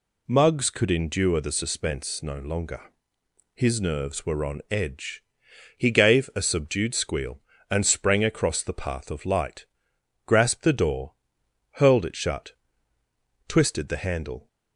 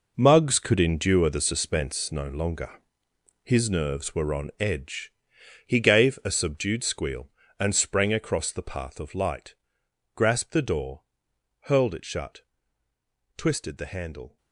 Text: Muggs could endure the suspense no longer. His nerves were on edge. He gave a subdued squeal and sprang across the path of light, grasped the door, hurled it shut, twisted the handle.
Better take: first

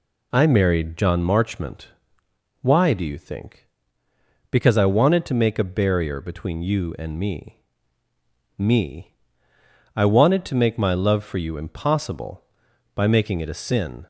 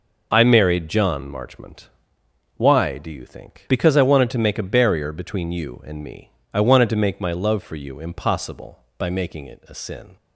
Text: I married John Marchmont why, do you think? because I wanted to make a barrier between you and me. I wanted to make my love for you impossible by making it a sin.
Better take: second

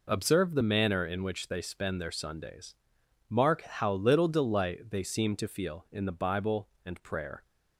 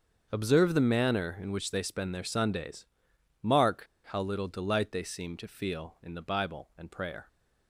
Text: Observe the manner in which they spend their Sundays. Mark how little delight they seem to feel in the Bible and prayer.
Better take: first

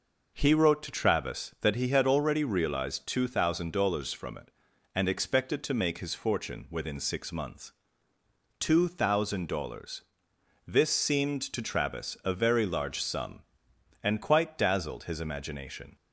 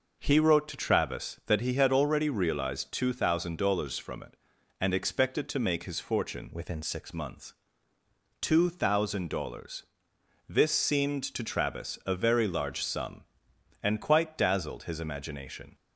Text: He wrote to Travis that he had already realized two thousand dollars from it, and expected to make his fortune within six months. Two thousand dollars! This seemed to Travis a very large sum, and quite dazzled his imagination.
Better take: first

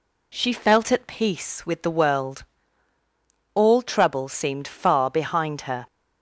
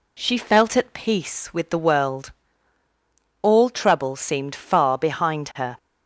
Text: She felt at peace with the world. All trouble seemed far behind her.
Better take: neither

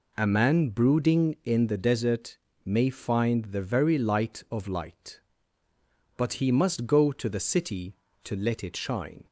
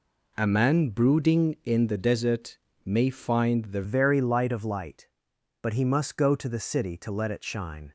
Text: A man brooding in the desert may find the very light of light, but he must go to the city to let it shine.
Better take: first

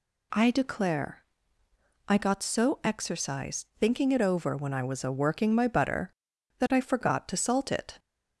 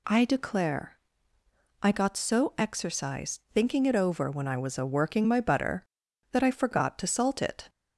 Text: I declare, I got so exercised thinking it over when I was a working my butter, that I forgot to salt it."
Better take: neither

